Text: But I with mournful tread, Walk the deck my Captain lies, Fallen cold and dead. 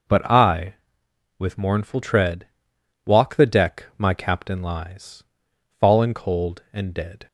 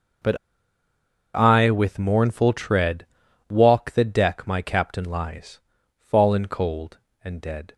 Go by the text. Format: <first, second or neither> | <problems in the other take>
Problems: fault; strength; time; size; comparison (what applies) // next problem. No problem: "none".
first | pauses between "But" and "I"; noticeable; at 0.3 s; 0.97 s long